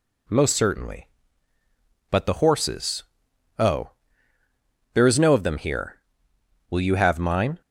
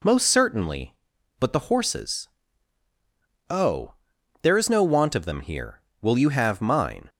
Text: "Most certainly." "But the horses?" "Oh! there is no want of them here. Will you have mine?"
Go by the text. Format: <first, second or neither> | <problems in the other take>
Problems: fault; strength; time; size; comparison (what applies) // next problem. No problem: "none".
second | skips "want"; at 5.3 s